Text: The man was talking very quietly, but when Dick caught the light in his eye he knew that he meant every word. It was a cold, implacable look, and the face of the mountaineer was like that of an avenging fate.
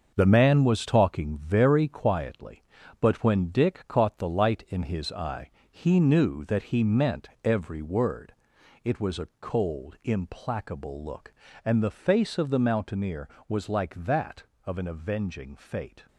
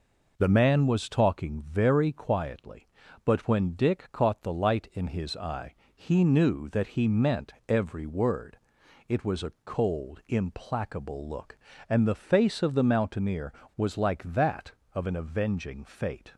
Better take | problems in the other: second | gets quieter; strong; throughout; 7.5 dB // pauses between "eye" and "he"; slight; at 5.5 s; 0.20 s long; slight in the second // pauses between "meant" and "every"; slight; at 7.2 s; 0.16 s long; slight in the second

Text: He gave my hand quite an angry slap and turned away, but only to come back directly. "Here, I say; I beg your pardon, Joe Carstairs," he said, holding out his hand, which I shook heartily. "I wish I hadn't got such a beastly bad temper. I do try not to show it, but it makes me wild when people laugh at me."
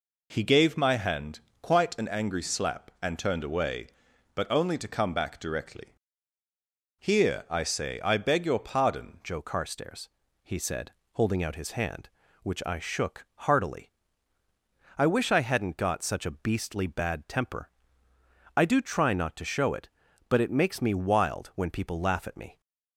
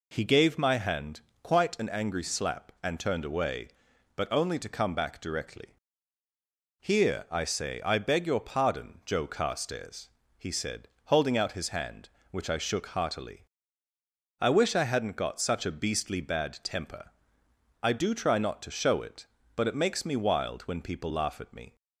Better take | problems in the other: second | pauses between "hand" and "quite"; slight; at 1.4 s; 0.20 s long; slight in the second // changes voice at "Joe"; from 9.2 s on; 13.4 s long // pauses between "shook" and "heartily"; slight; at 13.2 s; 0.22 s long

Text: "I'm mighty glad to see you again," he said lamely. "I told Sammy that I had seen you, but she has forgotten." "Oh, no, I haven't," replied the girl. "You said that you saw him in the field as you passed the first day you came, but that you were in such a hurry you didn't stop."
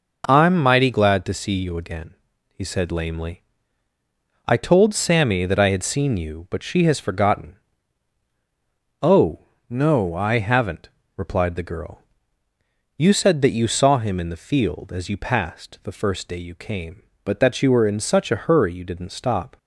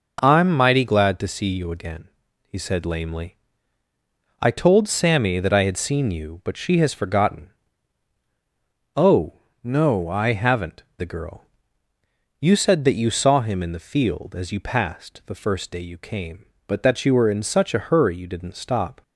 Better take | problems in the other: first | skips "replied"; at 10.9 s

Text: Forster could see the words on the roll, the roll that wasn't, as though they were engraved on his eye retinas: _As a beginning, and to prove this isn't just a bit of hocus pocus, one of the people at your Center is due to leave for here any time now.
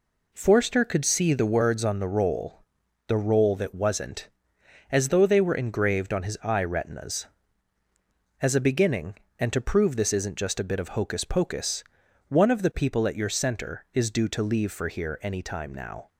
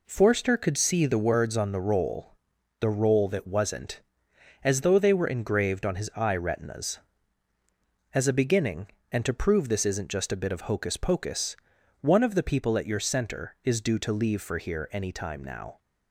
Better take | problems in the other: neither | none

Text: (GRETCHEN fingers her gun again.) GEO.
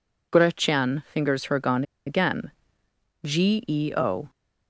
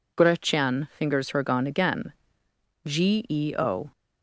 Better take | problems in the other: second | pauses between "gun" and "again"; slight; at 1.8 s; 0.24 s long

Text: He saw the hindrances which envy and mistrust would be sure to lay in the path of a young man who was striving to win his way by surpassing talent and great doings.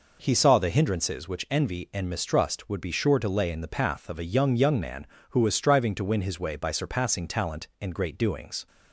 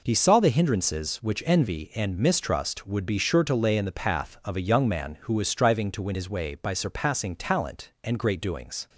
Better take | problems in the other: second | says "young" twice; at 4.5 s

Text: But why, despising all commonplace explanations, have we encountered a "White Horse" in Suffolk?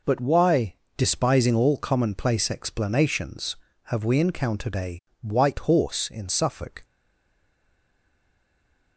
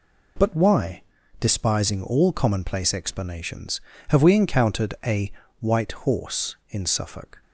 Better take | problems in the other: second | pauses between "a" and "White"; slight; at 4.9 s; 0.22 s long; slight in the second // stays silent after the last word; from 6.8 s on; 2.1 s long

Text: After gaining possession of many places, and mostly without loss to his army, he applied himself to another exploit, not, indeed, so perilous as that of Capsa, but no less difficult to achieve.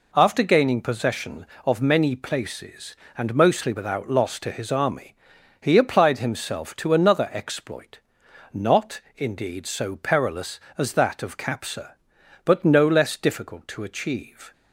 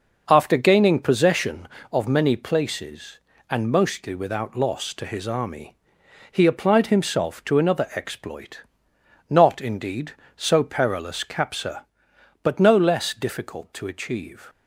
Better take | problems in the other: first | skips "as that of"; at 11.2 s

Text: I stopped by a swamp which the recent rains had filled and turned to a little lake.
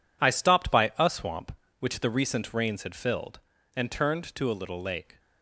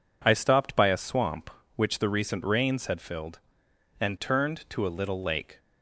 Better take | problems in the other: second | gets quieter; strong; throughout; 11 dB

